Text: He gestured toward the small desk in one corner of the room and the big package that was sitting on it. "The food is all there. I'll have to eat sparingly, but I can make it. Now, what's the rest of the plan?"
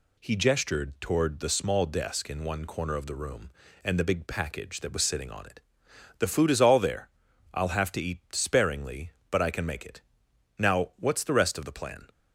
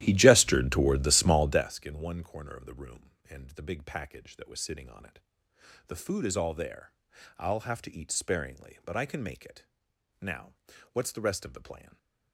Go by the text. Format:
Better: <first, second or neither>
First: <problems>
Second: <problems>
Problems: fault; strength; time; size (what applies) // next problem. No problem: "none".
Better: first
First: none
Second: starts louder than the rest; strong; until 1.8 s; 13.5 dB // stays silent after the last word; slight; from 11.8 s on; 0.5 s long